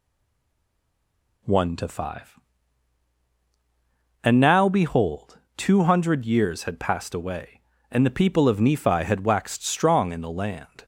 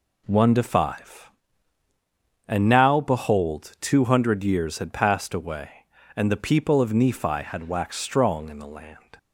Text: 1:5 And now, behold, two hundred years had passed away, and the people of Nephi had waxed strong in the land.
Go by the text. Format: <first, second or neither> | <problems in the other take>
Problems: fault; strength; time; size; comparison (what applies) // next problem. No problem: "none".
second | stays silent before the first word; noticeable; until 1.4 s; 1.4 s long